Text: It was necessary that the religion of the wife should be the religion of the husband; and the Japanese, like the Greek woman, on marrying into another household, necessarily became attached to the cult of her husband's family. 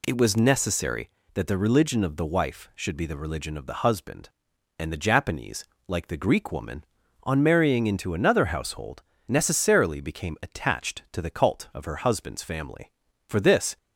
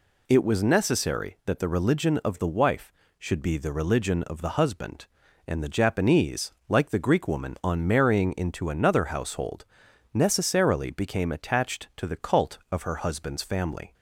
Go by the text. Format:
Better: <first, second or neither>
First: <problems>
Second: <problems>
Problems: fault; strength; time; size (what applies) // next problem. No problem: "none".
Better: second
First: goes on to say "For this"; from 13.2 s on; 0.50 s long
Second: none